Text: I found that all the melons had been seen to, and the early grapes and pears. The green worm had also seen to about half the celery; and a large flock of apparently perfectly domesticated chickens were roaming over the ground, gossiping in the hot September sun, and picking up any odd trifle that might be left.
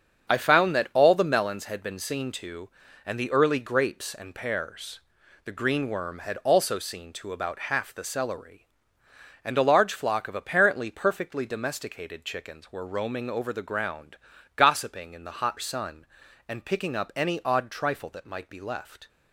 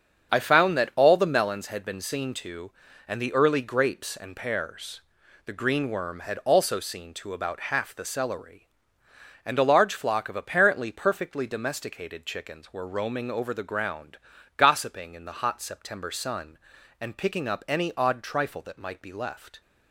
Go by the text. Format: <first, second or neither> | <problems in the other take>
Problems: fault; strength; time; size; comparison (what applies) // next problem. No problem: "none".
second | starts louder than the rest; strong; until 1.3 s; 7 dB; strong in the second // skips "September"; at 15.5 s